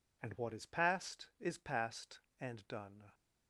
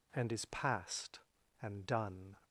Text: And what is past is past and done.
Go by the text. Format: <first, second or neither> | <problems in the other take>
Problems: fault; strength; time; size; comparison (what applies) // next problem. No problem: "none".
first | skips "what is past"; at 0.3 s